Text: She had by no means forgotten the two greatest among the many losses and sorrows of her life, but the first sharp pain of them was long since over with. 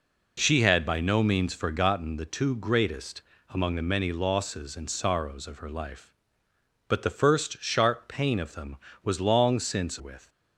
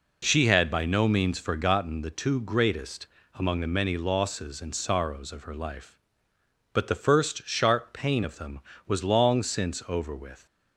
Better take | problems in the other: second | pauses between "greatest" and "among"; slight; at 3.2 s; 0.26 s long; slight in the second // skips "over"; at 9.9 s

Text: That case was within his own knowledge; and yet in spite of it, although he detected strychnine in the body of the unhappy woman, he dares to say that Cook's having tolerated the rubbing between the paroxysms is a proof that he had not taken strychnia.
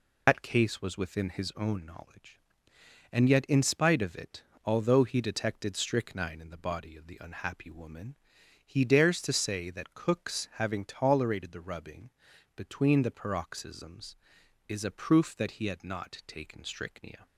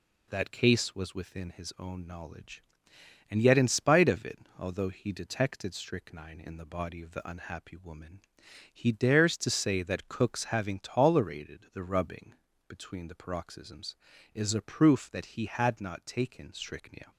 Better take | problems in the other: second | loses the start of "That"; at 0.2 s; 100 ms // pauses between "rubbing" and "between"; at 12.1 s; 0.44 s long; slight in the second

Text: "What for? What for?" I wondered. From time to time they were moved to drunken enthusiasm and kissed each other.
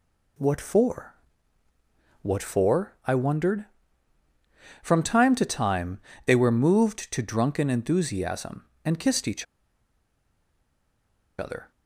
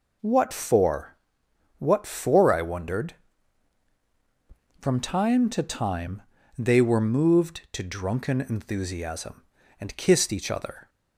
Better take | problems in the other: second | pauses between "time" and "they"; slight; at 5.9 s; 0.26 s long; slight in the second // pauses between "each" and "other"; strong; at 9.4 s; 1.9 s long

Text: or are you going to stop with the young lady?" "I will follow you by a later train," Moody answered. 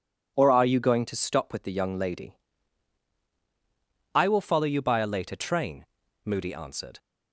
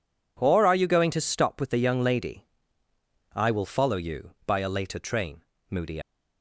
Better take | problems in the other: first | stops before "answered"; at 6.0 s

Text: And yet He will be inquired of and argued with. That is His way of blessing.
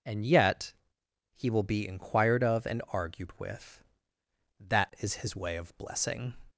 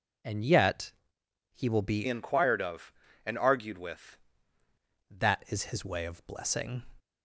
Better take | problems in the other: first | pauses between "yet" and "He"; noticeable; at 0.9 s; 0.62 s long; noticeable in the first // changes voice from "inquired" to "with"; from 2.0 to 4.1 s; 2.1 s long

